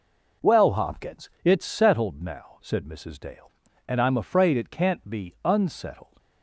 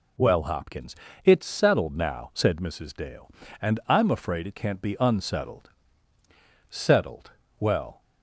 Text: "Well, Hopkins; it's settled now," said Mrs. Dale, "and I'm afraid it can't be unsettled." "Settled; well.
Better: second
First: stops before "Settled well"; at 6.1 s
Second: none

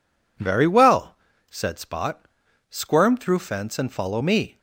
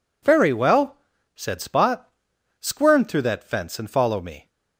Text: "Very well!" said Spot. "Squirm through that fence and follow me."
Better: second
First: skips "that"; at 3.3 s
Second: none

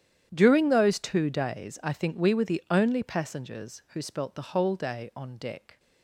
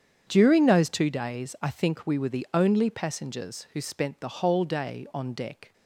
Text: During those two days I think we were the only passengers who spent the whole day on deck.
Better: second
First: starts louder than the rest; strong; until 1.3 s; 10 dB // says "spelt" for "spent"; at 4.0 s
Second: starts louder than the rest; strong; until 1.2 s; 8 dB

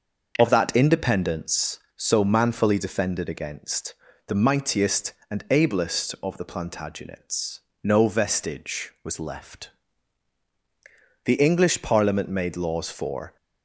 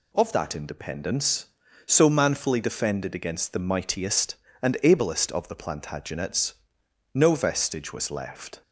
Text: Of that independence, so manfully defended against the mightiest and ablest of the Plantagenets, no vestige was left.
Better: second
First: starts louder than the rest; until 1.3 s; 6.5 dB // pauses between "against" and "the"; slight; at 3.9 s; 0.34 s long // goes on to say "The English Parliament made laws for"; strong; from 11.2 s on; 2.1 s long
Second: none

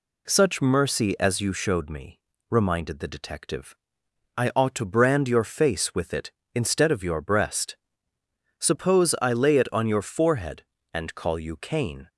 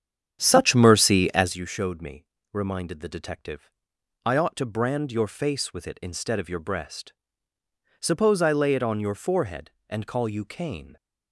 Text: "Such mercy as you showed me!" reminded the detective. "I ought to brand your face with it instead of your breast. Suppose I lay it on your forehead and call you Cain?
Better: first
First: none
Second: starts louder than the rest; strong; until 1.5 s; 9 dB

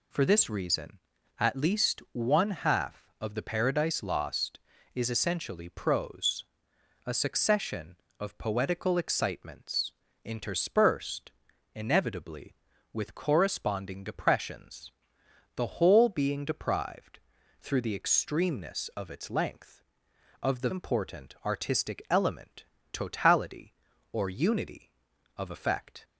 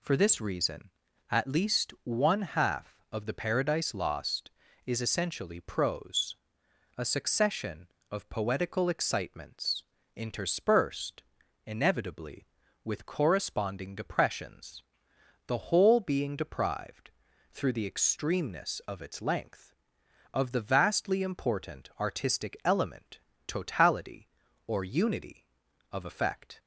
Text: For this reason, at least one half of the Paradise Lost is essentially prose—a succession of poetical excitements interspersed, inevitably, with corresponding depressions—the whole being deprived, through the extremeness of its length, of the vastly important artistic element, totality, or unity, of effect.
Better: second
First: pauses between "excitements" and "interspersed"; slight; at 9.9 s; 0.32 s long // skips "vastly"; at 20.6 s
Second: pauses between "excitements" and "interspersed"; slight; at 9.8 s; 0.32 s long

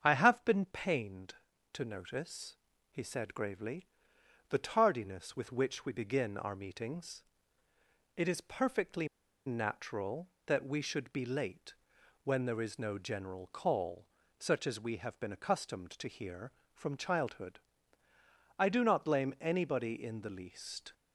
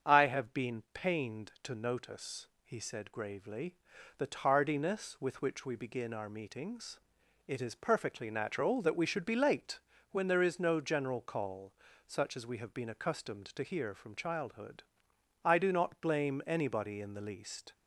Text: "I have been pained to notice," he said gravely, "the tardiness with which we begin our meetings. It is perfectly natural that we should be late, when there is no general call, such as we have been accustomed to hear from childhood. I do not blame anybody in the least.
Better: second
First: starts louder than the rest; strong; until 1.0 s; 7.5 dB // pauses between "perfectly" and "natural"; at 9.0 s; 0.39 s long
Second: starts louder than the rest; strong; until 1.1 s; 7 dB

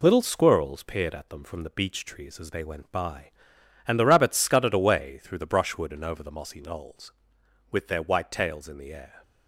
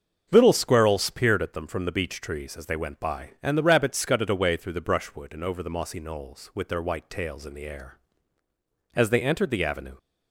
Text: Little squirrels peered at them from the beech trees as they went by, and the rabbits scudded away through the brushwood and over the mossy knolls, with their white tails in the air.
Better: first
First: none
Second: starts louder than the rest; until 1.3 s; 7 dB // goes on to say "As they entered the avenue"; noticeable; from 8.9 s on; 1.0 s long

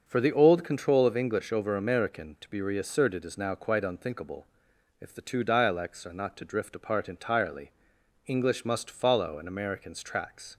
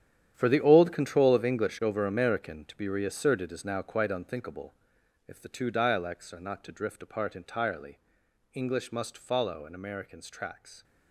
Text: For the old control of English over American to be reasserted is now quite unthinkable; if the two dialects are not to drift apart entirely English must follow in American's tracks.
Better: first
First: starts louder than the rest; noticeable; until 1.0 s; 6 dB // pauses between "entirely" and "English"; noticeable; at 7.7 s; 0.56 s long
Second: gets quieter; strong; throughout; 13.5 dB // starts louder than the rest; strong; until 1.3 s; 9.5 dB // pauses between "entirely" and "English"; noticeable; at 7.9 s; 0.56 s long

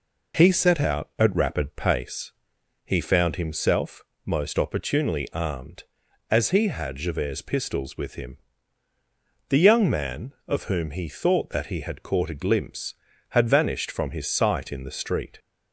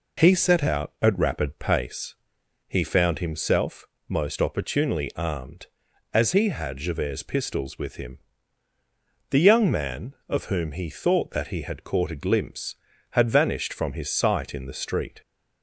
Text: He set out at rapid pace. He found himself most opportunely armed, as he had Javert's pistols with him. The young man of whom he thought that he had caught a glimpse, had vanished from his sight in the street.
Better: neither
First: pauses between "himself" and "most"; slight; at 4.0 s; 0.22 s long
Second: pauses between "himself" and "most"; slight; at 3.8 s; 0.22 s long

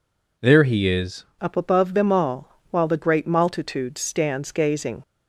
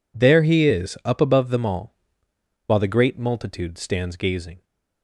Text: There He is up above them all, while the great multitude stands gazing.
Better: second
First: changes voice at "up"; from 1.3 s on; 3.7 s long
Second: none

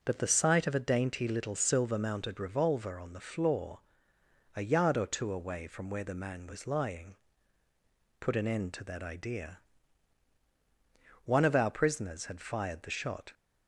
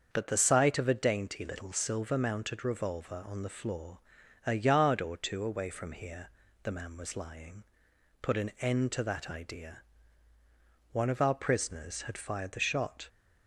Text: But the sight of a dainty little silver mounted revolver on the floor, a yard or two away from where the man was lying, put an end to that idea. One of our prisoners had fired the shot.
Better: first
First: none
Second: starts louder than the rest; until 1.1 s; 7 dB // says "here" for "where"; at 5.9 s

